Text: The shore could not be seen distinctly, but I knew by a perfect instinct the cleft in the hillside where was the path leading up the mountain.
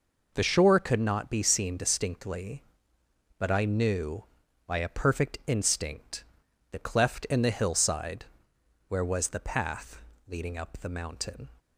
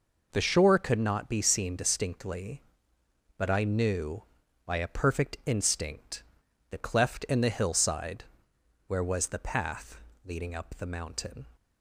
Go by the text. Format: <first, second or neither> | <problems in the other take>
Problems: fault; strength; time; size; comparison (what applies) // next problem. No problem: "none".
neither | pauses between "instinct" and "the"; noticeable; the same in both // pauses between "hillside" and "where"; noticeable; the same in both // pauses between "path" and "leading"; slight; the same in both